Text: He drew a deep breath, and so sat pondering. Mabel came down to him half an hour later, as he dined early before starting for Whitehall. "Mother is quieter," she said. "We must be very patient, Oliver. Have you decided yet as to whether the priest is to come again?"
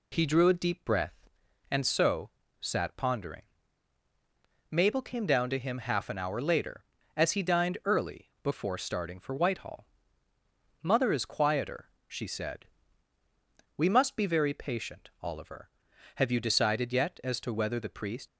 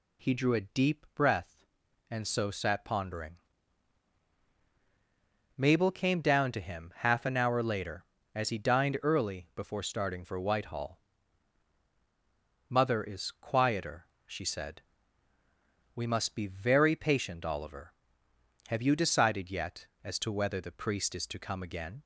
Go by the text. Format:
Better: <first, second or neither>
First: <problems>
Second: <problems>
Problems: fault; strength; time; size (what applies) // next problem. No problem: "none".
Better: second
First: pauses between "so" and "sat"; slight; at 2.2 s; 0.32 s long // stops before "is to come again"; at 18.2 s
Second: none